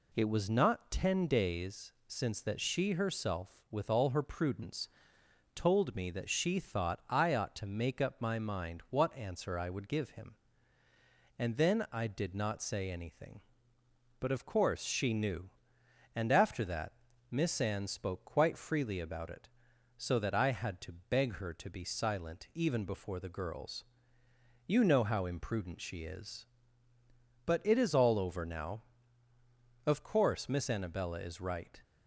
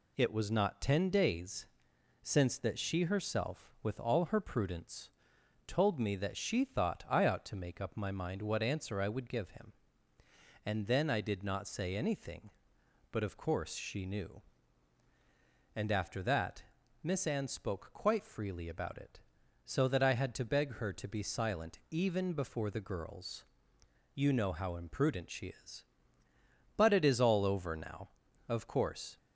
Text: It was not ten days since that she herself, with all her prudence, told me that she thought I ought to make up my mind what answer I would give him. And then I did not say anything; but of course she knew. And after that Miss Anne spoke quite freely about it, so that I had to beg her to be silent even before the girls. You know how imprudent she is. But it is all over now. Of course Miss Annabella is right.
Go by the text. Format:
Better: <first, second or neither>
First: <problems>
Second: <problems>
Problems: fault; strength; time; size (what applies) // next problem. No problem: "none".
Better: first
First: pauses between "days" and "since"; slight; at 1.9 s; 0.16 s long // pauses between "that" and "Miss"; at 16.9 s; 0.38 s long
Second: pauses between "days" and "since"; noticeable; at 1.6 s; 0.56 s long // pauses between "that" and "Miss"; at 16.6 s; 0.40 s long // stops before "Miss Annabella is right"; at 29.1 s